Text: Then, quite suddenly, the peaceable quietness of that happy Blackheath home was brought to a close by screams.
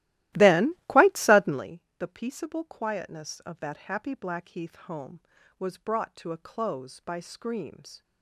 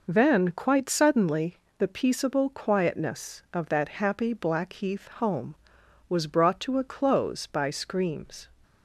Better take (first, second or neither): second